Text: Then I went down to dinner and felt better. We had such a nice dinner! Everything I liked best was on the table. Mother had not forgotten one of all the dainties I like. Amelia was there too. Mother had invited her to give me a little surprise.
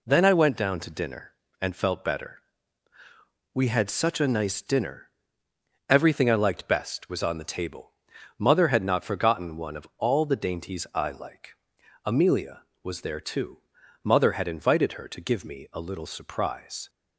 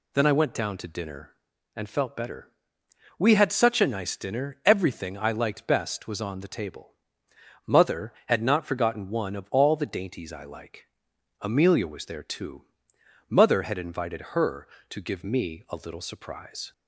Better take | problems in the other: neither | none

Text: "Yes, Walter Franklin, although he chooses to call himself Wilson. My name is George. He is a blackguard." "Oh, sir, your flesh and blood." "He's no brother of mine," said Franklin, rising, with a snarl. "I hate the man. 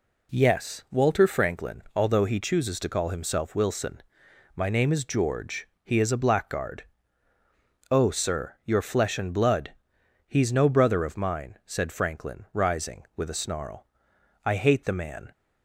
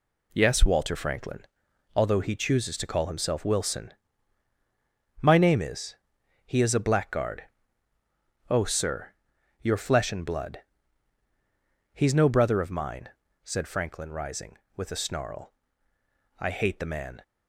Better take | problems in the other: first | skips "George"; at 6.2 s

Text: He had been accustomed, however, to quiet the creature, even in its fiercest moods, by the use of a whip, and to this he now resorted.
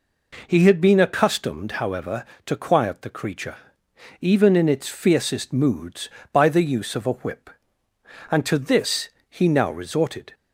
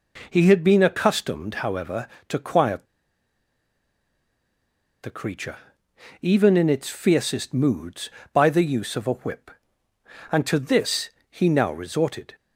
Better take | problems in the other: first | pauses between "quiet" and "the"; strong; at 2.8 s; 2.1 s long // pauses between "this" and "he"; slight; at 11.0 s; 0.20 s long; slight in the first

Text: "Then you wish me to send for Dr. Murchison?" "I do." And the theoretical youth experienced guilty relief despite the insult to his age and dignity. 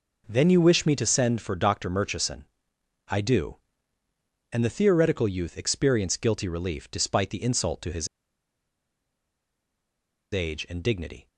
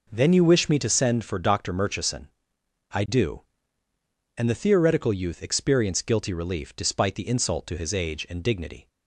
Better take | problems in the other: second | pauses between "his" and "age"; strong; at 8.0 s; 2.2 s long

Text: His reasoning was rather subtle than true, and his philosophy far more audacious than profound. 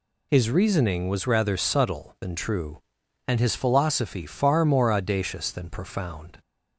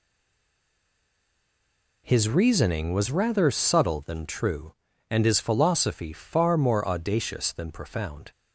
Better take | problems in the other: first | stays silent before the first word; noticeable; until 2.0 s; 2.0 s long

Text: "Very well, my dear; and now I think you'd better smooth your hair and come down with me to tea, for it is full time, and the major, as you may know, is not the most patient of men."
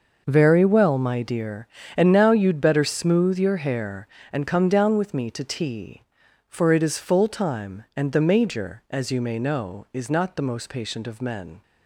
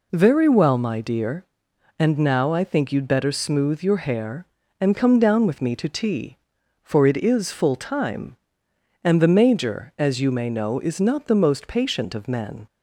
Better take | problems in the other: second | skips "I think"; at 2.2 s

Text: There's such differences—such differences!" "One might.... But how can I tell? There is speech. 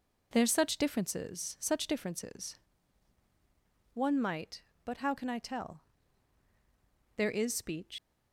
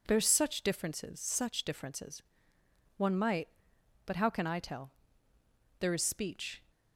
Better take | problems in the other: second | leaves "speech" unfinished; at 7.9 s; 125 ms

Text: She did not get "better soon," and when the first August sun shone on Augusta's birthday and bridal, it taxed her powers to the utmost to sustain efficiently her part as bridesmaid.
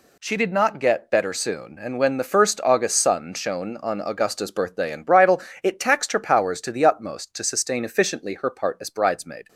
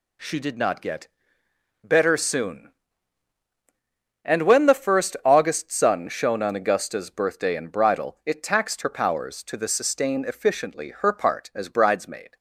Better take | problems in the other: first | pauses between "get" and "better"; noticeable; at 1.0 s; 0.74 s long // skips "utmost to"; at 9.6 s

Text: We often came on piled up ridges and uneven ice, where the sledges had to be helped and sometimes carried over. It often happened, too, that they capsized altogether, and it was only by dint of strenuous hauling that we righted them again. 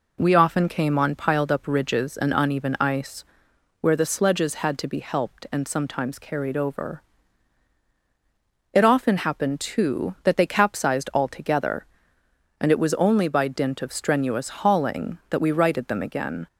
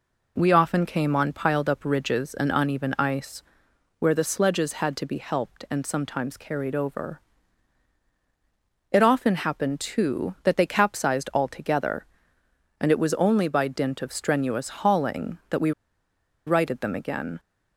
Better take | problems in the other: first | pauses between "we" and "righted"; noticeable; at 15.7 s; 0.75 s long

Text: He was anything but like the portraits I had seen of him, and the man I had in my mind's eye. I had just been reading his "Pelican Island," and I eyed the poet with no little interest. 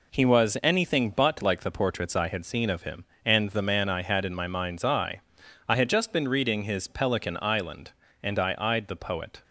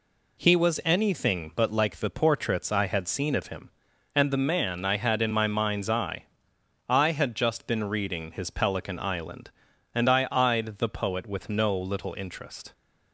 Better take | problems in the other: second | stops before "with no little interest"; at 9.4 s

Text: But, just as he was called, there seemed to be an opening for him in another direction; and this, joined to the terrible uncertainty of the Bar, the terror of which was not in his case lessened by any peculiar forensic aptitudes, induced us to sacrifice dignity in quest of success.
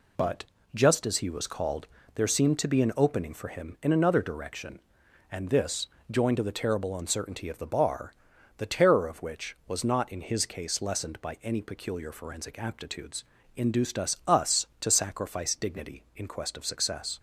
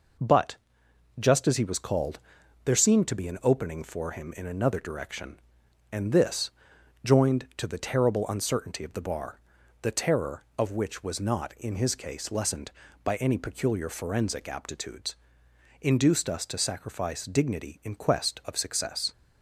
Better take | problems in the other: second | says "us" twice; at 14.2 s

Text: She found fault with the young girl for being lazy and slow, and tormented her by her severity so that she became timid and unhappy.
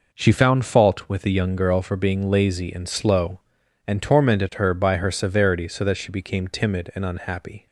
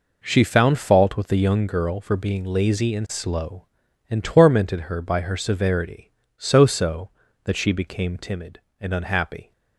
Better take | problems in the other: first | says "so" twice; at 6.6 s

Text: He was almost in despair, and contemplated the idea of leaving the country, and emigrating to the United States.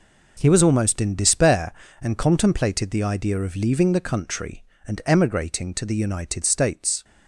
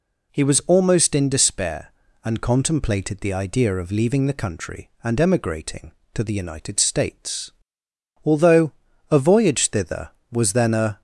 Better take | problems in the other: first | goes on to say "Although a voyage thither was then a"; strong; from 8.2 s on; 2.7 s long

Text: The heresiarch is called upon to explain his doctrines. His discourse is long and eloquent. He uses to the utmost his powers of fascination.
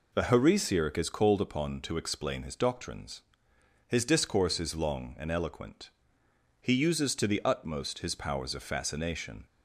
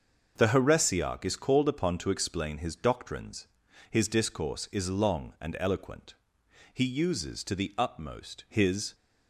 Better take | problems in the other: first | starts louder than the rest; until 1.3 s; 6.5 dB // stops before "powers of fascination"; at 8.9 s

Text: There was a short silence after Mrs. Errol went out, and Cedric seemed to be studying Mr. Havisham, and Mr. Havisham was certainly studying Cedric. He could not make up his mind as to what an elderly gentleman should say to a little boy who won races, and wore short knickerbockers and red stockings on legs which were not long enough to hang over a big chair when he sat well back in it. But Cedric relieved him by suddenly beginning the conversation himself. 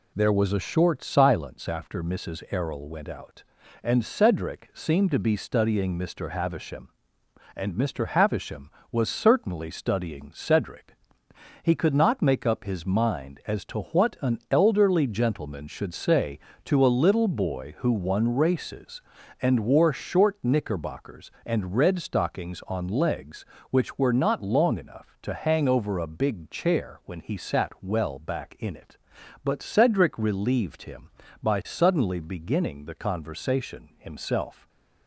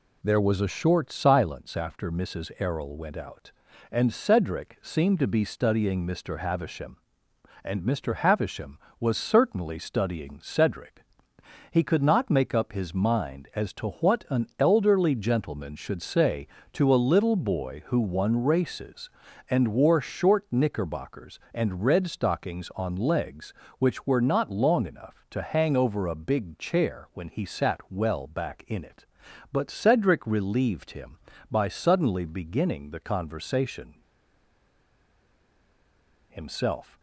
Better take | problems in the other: first | pauses between "conversation" and "himself"; strong; at 33.9 s; 2.3 s long

